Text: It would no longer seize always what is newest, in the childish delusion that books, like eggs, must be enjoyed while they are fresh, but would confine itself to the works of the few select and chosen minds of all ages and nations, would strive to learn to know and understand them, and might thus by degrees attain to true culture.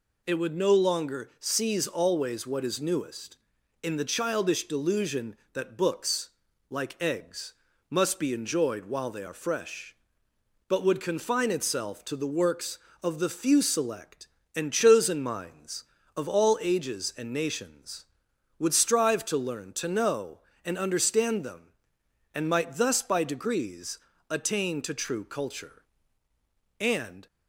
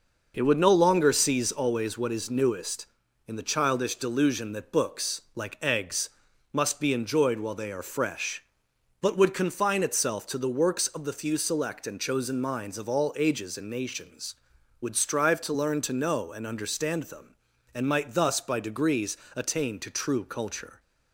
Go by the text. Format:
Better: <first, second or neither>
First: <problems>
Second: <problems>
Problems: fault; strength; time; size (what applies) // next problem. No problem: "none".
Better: second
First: pauses between "degrees" and "attain"; slight; at 23.9 s; 0.32 s long // goes on to say "And"; slight; from 26.7 s on; 0.48 s long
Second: pauses between "degrees" and "attain"; slight; at 19.1 s; 0.20 s long